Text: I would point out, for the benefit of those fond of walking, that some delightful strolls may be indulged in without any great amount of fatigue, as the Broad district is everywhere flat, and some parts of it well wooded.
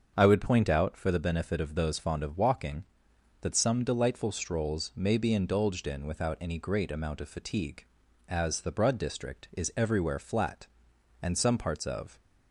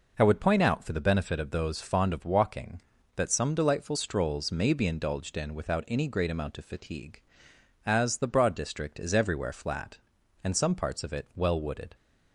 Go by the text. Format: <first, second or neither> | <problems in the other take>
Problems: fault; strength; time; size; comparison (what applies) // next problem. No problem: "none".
second | starts louder than the rest; until 1.1 s; 7 dB // stops before "it well wooded"; at 12.1 s